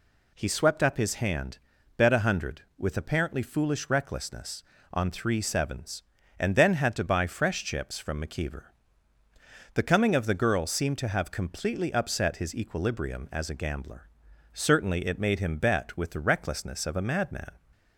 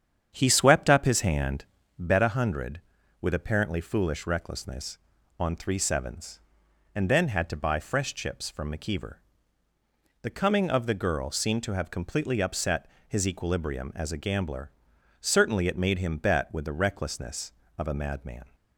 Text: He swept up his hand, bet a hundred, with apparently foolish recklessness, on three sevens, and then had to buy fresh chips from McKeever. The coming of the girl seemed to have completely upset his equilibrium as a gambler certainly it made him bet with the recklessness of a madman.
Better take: first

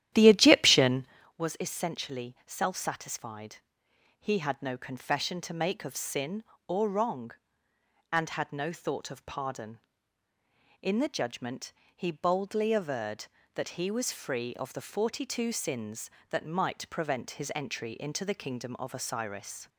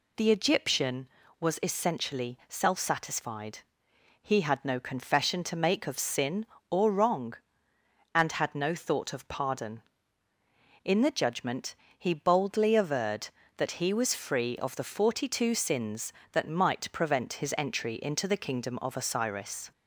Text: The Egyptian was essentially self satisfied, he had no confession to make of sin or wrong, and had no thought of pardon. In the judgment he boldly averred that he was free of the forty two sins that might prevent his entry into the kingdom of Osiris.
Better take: second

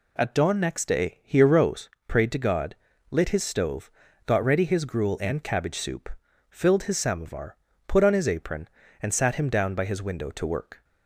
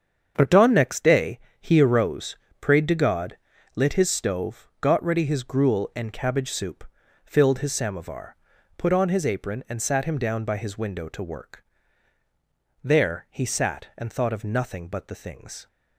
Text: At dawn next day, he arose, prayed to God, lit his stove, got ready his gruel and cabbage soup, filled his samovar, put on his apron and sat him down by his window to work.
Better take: first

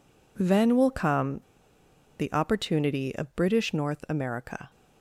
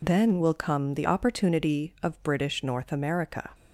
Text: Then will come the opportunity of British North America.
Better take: second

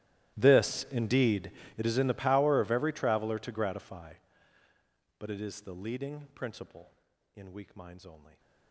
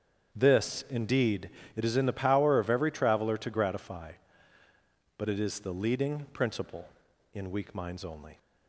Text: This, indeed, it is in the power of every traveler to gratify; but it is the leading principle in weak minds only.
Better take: second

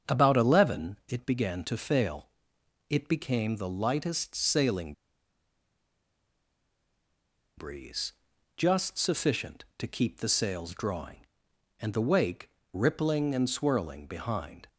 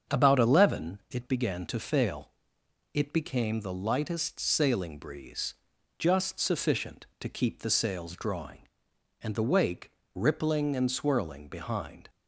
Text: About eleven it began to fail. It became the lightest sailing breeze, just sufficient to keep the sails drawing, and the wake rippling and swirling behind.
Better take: second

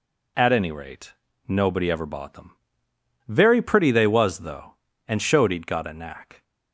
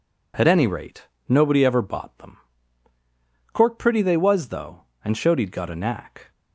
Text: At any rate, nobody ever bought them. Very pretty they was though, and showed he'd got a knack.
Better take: first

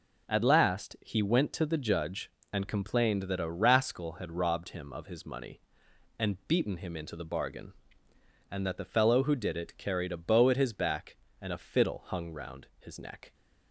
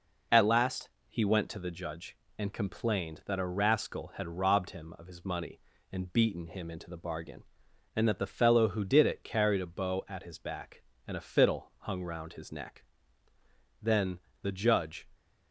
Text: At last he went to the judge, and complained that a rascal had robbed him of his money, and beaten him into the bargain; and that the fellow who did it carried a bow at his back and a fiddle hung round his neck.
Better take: first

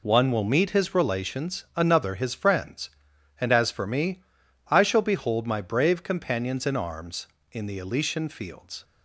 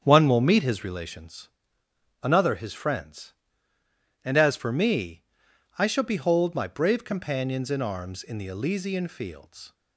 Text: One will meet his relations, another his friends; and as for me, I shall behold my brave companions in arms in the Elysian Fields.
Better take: first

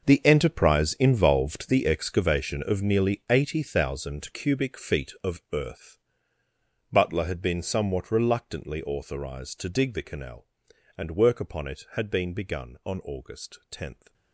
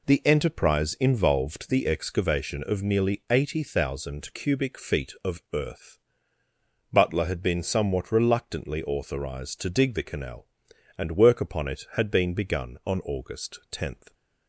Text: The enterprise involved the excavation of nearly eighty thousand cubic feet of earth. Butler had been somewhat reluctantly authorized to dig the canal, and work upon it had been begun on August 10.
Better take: second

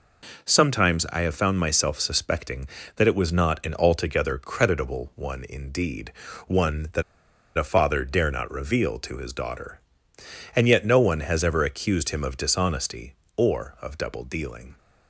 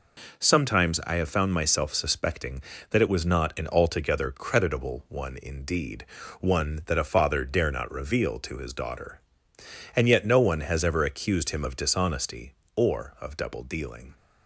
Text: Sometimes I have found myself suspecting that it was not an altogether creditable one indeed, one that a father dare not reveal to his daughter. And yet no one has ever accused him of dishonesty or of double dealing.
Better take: second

